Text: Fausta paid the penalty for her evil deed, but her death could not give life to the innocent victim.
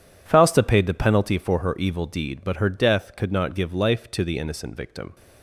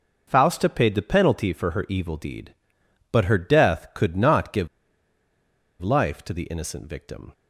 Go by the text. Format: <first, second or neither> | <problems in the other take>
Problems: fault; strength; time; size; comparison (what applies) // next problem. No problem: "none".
first | pauses between "give" and "life"; at 4.6 s; 1.1 s long